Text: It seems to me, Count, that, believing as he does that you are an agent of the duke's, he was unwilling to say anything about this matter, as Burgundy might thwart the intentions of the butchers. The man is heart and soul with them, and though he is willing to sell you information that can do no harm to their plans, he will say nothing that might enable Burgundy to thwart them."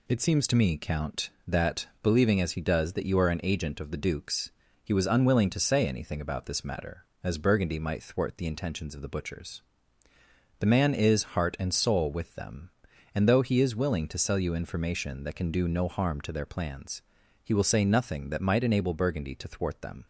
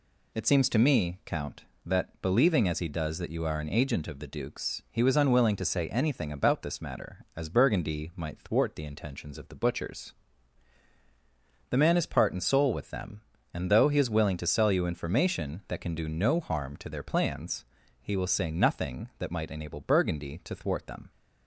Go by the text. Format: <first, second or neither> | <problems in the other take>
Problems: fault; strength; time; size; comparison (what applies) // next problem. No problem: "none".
first | says "part" for "heart"; at 12.0 s